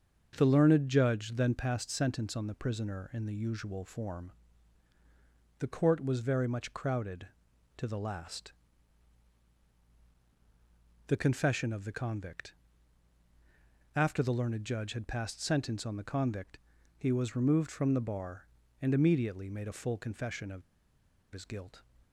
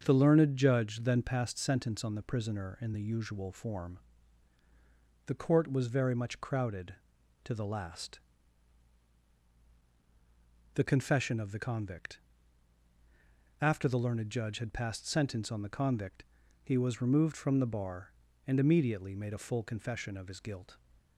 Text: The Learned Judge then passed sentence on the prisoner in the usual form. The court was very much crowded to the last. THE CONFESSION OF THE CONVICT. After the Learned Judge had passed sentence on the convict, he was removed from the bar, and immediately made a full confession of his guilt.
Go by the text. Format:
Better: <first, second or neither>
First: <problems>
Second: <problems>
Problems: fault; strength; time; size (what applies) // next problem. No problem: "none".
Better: second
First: starts louder than the rest; until 1.3 s; 6.5 dB // pauses between "of" and "his"; noticeable; at 20.6 s; 0.70 s long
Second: starts louder than the rest; until 1.0 s; 6.5 dB